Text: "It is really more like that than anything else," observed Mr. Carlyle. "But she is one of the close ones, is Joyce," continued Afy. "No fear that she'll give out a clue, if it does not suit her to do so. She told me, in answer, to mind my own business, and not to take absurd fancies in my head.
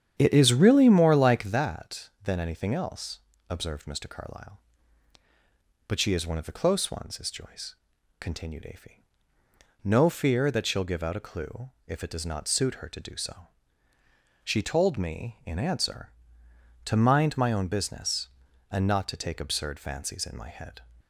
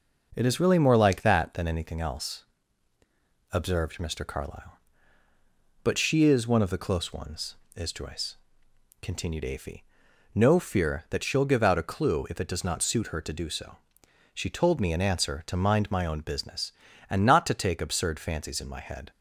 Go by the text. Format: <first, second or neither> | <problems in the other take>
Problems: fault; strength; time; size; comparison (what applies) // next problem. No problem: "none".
second | starts louder than the rest; strong; until 1.6 s; 9 dB